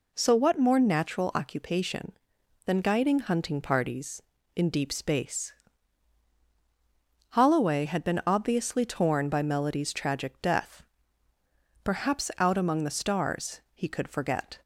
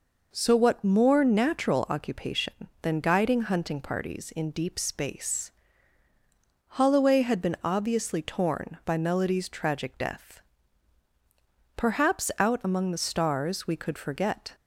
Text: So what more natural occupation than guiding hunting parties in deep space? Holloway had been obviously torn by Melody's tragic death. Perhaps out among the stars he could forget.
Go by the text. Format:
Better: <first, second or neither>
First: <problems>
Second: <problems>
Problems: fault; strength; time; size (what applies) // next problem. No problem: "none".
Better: first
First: none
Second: says "we" for "he"; at 13.6 s